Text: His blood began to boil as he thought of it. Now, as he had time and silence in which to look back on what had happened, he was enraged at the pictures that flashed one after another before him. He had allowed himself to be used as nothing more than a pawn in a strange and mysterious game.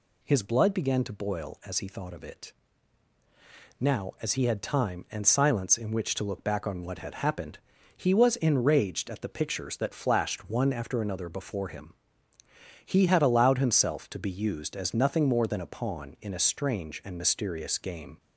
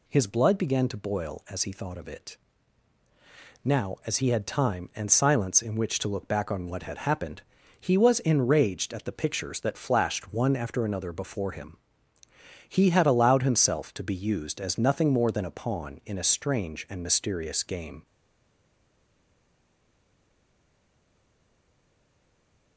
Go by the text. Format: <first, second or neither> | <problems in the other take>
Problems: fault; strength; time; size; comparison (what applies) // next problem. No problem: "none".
first | stays silent after the last word; strong; from 18.0 s on; 4.7 s long